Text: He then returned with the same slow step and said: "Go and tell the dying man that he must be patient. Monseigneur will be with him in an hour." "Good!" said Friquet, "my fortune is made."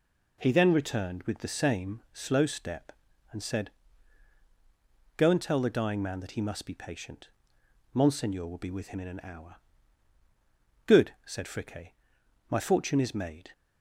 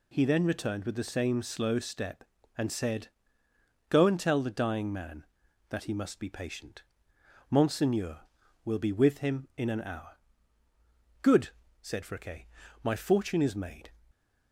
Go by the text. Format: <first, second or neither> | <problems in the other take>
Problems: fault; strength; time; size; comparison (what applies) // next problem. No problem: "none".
neither | none